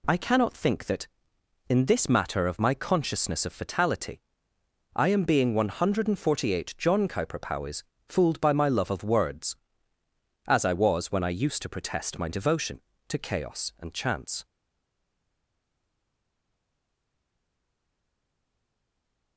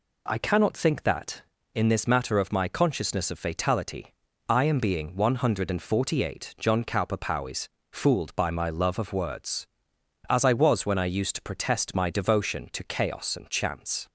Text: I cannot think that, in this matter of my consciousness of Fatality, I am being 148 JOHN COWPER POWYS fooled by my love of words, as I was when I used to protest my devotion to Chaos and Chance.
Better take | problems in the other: second | pauses between "POWYS" and "fooled"; slight; at 7.8 s; 0.24 s long; slight in the second // stays silent after the last word; strong; from 14.4 s on; 4.9 s long

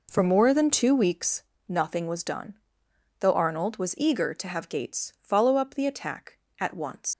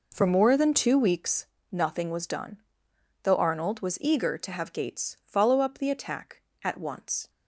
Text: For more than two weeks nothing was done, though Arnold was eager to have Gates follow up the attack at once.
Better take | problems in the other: second | pauses between "weeks" and "nothing"; slight; at 1.4 s; 0.24 s long; slight in the second // leaves "once" unfinished; at 7.1 s; 125 ms

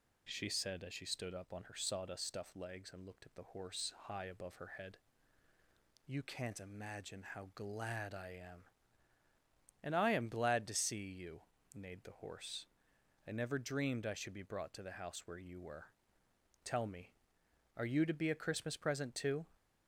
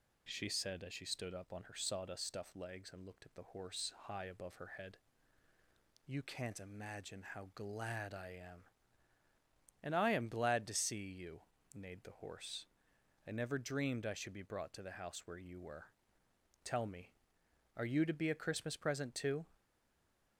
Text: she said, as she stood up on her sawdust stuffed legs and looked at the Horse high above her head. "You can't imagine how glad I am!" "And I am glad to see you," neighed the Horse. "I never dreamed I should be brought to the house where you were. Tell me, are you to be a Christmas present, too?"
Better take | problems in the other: first | stays silent after the last word; slight; from 19.5 s on; 0.8 s long

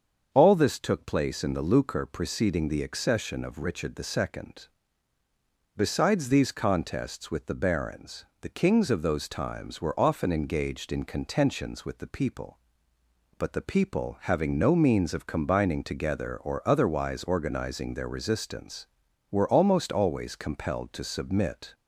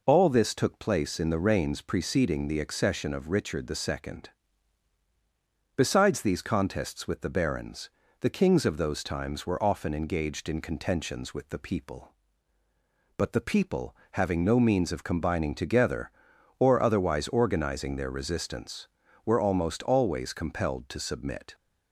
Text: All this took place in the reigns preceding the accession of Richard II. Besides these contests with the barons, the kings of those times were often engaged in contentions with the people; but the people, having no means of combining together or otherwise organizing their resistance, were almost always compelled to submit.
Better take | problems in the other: second | starts louder than the rest; until 1.3 s; 7 dB // says "lucre" for "reigns"; at 1.6 s

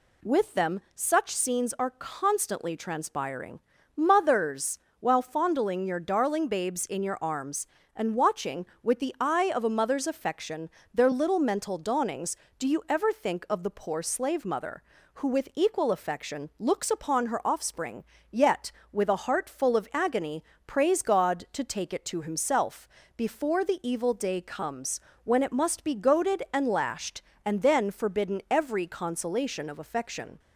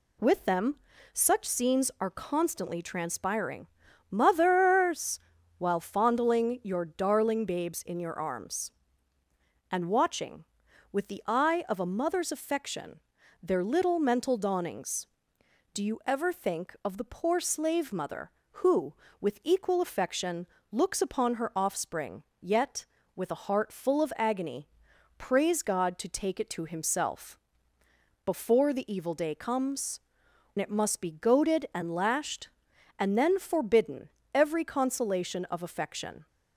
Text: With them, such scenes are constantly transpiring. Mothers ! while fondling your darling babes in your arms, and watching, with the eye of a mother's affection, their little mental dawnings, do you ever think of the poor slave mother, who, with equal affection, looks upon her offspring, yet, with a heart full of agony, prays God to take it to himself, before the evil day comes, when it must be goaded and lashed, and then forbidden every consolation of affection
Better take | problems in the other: first | skips "when"; at 30.2 s // pauses between "forbidden" and "every"; slight; at 34.0 s; 0.26 s long

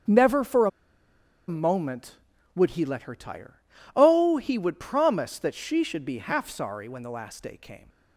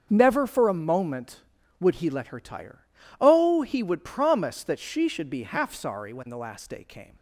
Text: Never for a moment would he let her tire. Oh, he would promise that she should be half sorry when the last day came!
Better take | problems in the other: second | starts louder than the rest; strong; until 1.8 s; 7 dB; strong in the second // pauses between "a" and "moment"; noticeable; at 0.6 s; 0.78 s long

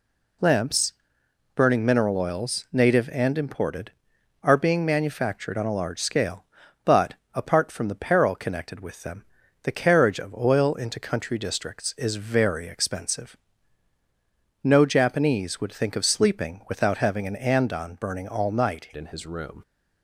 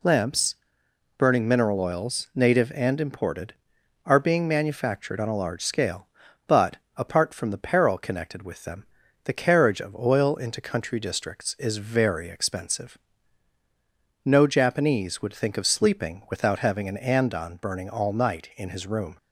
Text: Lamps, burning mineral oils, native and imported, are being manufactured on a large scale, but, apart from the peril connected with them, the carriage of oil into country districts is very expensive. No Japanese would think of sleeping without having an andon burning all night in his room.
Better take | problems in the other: second | changes voice at "in"; from 18.9 s on; 0.7 s long

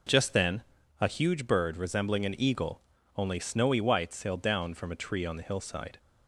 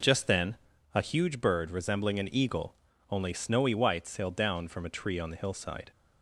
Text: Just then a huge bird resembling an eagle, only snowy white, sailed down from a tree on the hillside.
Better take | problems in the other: neither | pauses between "then" and "a"; the same in both

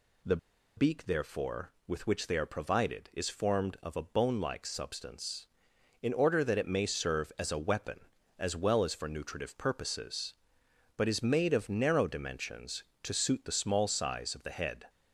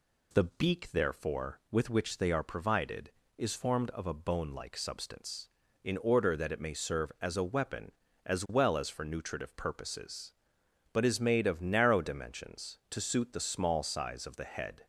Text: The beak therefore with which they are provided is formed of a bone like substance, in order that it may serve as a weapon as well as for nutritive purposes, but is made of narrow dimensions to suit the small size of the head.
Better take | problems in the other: second | pauses between "The" and "beak"; at 0.3 s; 0.40 s long

